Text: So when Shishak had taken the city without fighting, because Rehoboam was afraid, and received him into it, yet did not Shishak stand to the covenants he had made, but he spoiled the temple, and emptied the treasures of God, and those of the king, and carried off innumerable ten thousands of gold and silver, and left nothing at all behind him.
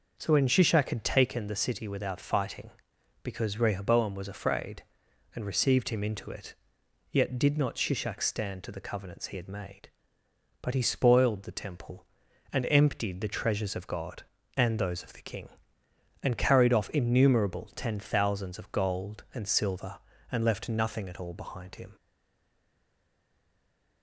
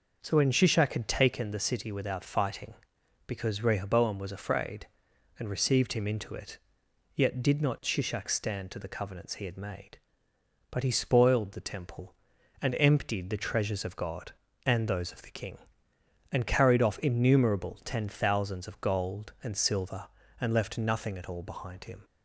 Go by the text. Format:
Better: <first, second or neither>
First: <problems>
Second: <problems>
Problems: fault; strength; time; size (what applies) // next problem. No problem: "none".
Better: second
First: stays silent after the last word; noticeable; from 21.9 s on; 2.1 s long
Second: none